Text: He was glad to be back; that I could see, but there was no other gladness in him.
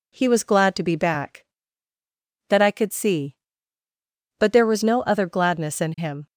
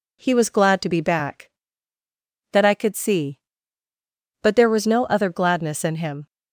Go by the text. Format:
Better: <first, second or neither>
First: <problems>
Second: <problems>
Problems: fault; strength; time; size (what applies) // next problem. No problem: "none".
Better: neither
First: none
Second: none